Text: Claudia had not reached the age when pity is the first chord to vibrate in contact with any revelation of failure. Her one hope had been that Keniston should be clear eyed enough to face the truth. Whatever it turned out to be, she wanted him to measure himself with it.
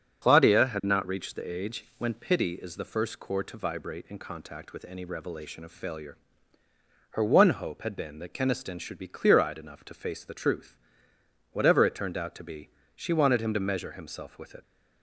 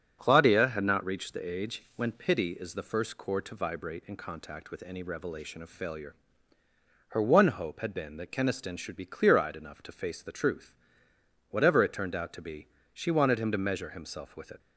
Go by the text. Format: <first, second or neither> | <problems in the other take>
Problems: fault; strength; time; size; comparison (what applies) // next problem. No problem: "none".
second | loses the start of "Claudia"; at 0.2 s; 40 ms // starts louder than the rest; until 1.3 s; 7 dB; strong in the second